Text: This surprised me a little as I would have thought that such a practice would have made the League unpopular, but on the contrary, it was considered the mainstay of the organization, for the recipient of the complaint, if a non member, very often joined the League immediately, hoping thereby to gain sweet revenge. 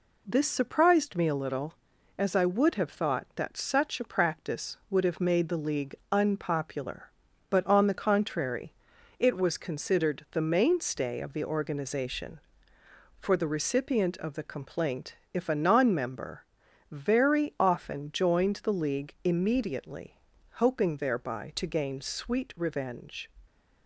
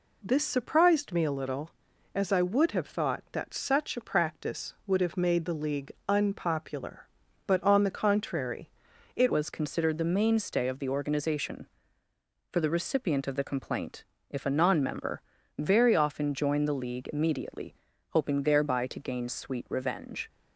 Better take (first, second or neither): first